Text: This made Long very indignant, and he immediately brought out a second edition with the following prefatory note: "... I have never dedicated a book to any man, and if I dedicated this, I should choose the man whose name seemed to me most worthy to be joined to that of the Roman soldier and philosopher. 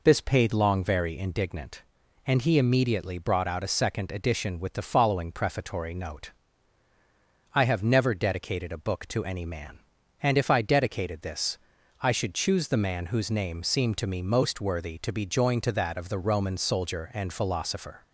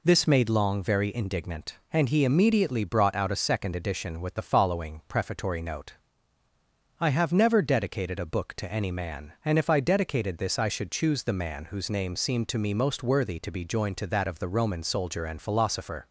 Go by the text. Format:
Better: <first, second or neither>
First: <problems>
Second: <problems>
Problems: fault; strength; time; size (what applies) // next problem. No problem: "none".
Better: second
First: says "paid" for "made"; at 0.2 s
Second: none